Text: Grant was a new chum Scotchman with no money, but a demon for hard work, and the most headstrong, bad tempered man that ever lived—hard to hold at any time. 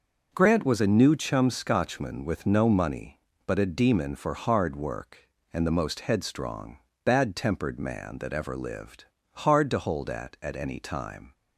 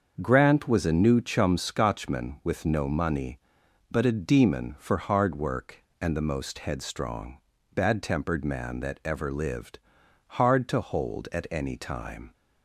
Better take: second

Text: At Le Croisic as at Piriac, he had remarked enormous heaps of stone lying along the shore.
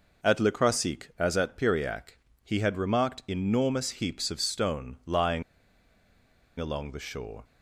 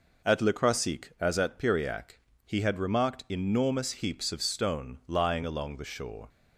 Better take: second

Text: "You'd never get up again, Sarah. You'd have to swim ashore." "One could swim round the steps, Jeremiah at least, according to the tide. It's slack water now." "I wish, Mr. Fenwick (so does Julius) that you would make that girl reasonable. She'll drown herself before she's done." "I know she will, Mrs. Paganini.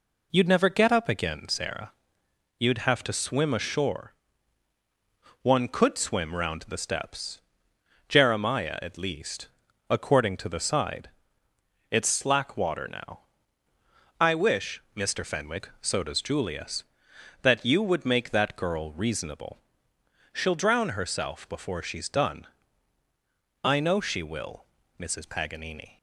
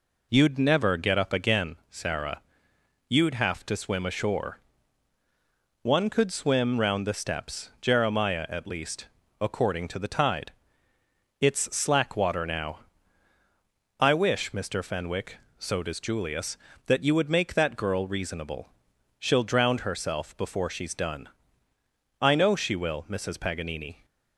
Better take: second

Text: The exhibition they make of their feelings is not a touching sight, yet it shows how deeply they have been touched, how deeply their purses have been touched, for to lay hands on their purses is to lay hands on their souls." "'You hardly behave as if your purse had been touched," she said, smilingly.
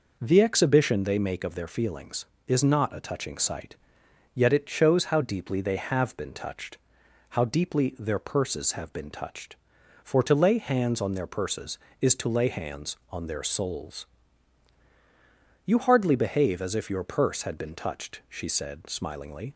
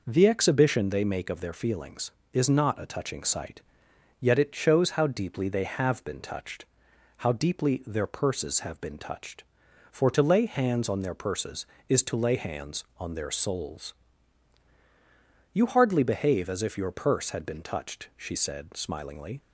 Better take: neither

